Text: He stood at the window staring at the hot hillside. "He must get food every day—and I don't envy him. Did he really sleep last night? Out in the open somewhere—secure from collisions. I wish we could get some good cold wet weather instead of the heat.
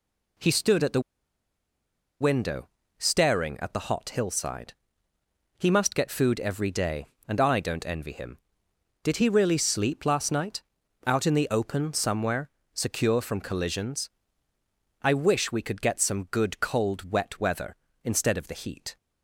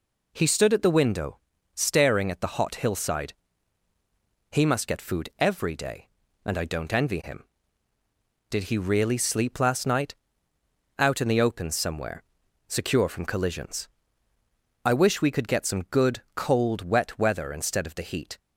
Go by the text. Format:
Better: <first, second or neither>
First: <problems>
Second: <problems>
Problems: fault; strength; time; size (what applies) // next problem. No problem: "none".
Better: second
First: pauses between "the" and "window"; at 0.9 s; 1.2 s long // pauses between "window" and "staring"; slight; at 2.6 s; 0.30 s long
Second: pauses between "window" and "staring"; slight; at 1.3 s; 0.36 s long